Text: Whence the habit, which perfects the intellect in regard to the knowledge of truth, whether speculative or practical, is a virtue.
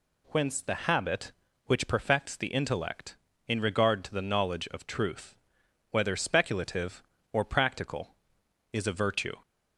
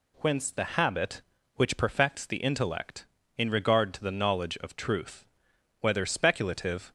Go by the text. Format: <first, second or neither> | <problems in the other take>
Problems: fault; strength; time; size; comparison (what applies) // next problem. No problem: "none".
first | stops before "or practical is a virtue"; at 6.8 s